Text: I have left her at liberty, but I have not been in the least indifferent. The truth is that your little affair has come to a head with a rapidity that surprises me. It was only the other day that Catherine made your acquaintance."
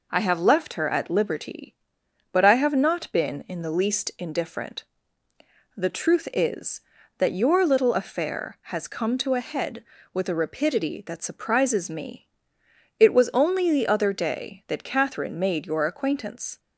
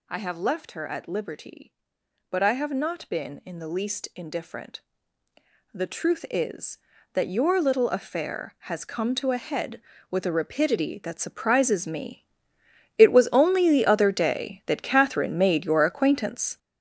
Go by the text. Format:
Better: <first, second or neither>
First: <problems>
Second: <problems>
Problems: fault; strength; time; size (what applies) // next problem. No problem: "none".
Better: first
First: none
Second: gets louder; strong; throughout; 9 dB